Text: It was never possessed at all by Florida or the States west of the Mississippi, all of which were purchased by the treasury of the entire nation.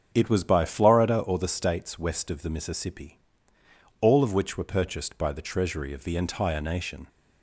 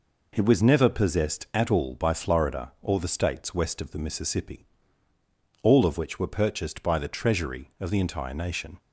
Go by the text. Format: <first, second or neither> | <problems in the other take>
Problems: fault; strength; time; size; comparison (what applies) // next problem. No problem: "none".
second | starts louder than the rest; strong; until 1.1 s; 7.5 dB // skips "never possessed at all"; at 0.4 s